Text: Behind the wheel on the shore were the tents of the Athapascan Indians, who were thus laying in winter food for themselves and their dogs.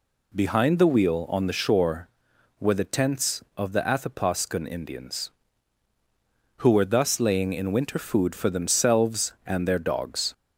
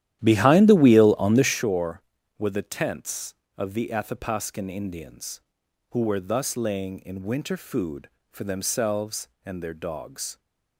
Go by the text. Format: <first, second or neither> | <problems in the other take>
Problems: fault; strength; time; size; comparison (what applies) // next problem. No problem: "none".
first | starts louder than the rest; strong; until 1.6 s; 12 dB